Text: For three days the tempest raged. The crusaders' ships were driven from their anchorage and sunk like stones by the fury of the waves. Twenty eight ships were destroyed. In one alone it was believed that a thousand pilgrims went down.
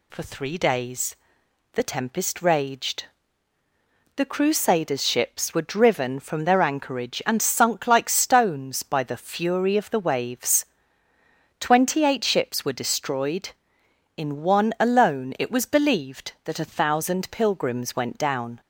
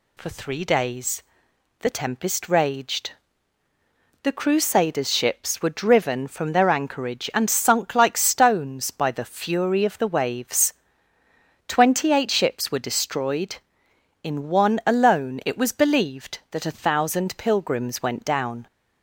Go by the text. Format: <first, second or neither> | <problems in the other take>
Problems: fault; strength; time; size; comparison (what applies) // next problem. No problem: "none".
neither | pauses between "days" and "the"; noticeable; the same in both